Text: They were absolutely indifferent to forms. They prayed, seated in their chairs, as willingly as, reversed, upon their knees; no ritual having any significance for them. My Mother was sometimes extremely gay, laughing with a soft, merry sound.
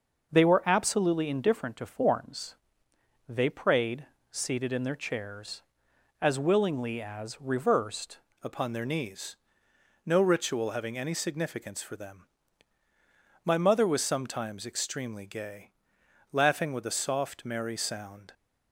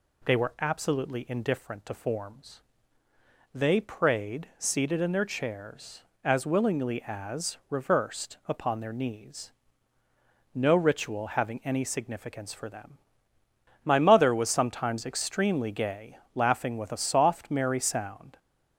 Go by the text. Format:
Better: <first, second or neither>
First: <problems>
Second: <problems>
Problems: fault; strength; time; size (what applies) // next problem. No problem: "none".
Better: second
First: changes voice at "upon"; from 8.4 s on; 9.9 s long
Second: none